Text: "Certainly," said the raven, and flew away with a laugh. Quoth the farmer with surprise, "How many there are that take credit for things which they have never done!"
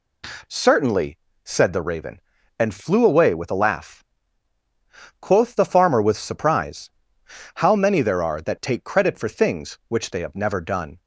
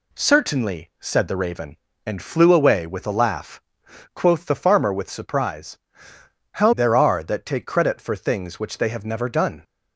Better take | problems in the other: first | skips "many"; at 6.7 s

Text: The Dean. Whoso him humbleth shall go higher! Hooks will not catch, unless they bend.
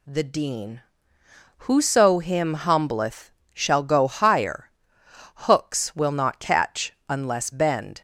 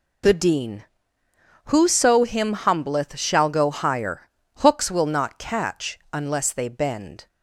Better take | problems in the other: second | pauses between "humbleth" and "shall"; slight; at 3.3 s; 0.22 s long // skips "they"; at 7.4 s

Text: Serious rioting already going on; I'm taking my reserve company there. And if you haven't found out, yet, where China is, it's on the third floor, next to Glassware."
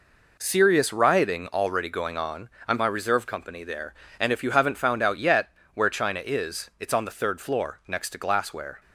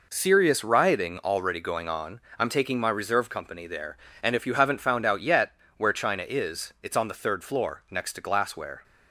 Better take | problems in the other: second | skips "taking"; at 2.7 s

